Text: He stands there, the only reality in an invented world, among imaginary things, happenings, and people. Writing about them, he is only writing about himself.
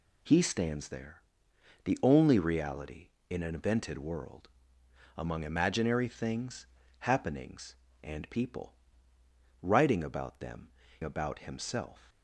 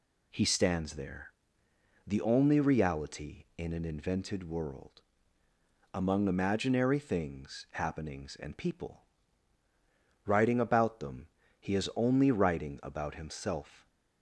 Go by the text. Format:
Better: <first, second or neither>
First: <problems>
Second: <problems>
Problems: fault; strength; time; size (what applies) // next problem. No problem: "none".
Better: second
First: skips "he is only writing"; at 10.8 s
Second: none